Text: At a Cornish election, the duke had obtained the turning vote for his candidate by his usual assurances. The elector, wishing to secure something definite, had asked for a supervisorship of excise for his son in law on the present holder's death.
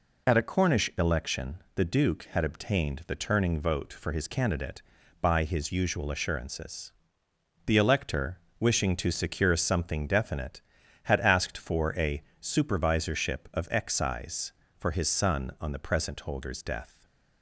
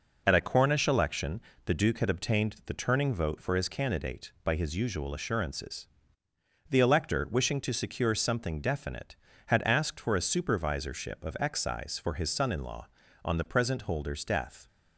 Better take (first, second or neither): second